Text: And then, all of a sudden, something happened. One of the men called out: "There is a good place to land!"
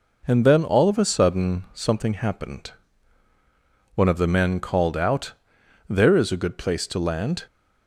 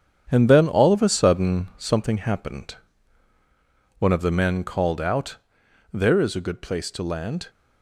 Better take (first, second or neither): first